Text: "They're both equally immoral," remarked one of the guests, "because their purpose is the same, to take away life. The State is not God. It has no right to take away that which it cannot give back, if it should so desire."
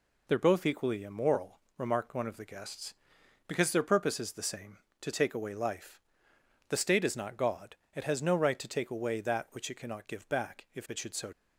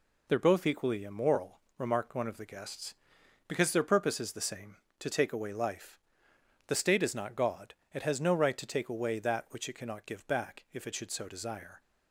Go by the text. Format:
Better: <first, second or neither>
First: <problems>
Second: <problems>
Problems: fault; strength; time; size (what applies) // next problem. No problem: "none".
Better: second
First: stops before "desire"; at 11.3 s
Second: none